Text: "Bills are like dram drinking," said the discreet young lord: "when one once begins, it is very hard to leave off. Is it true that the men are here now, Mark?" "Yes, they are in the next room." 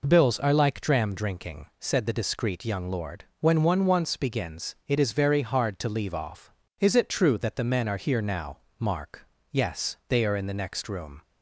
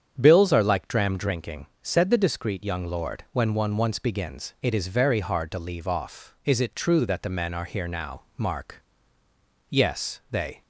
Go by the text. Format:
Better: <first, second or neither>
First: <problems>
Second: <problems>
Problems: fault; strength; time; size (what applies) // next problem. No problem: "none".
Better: first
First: none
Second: starts louder than the rest; strong; until 1.1 s; 8 dB // stops before "are in the next room"; at 10.6 s